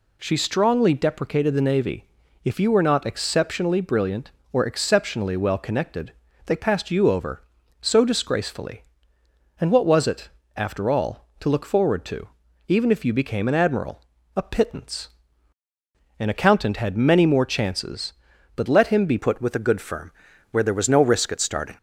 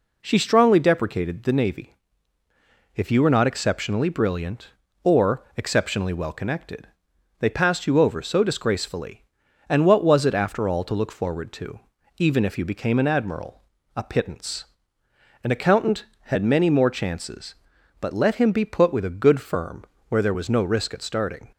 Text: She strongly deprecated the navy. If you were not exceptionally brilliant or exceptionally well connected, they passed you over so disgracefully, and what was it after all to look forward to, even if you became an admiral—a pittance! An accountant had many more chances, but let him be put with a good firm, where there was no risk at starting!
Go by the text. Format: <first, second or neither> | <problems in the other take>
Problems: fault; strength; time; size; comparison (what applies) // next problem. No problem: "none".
second | pauses between "it" and "after"; slight; at 10.2 s; 0.28 s long // changes voice at "put"; from 19.1 s on; 2.6 s long